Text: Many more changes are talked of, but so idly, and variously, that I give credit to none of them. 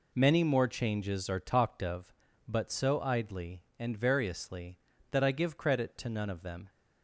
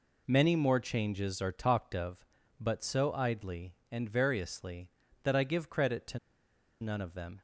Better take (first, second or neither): first